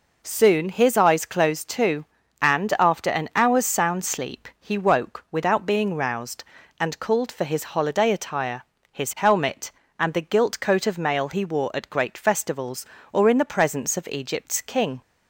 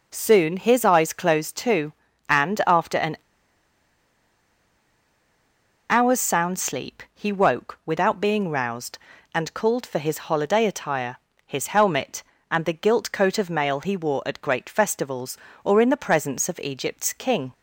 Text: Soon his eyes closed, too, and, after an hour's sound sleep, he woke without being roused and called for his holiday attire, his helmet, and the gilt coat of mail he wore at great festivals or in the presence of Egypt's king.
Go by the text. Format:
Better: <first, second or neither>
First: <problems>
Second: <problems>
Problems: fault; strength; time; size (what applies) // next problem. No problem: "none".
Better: first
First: none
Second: pauses between "an" and "hour's"; strong; at 3.1 s; 2.7 s long